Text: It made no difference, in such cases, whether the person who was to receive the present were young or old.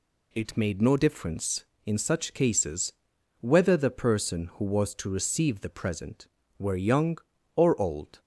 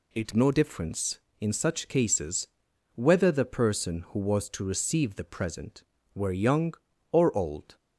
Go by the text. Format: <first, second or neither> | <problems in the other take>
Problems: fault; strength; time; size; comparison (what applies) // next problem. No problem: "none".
first | skips "made"; at 0.3 s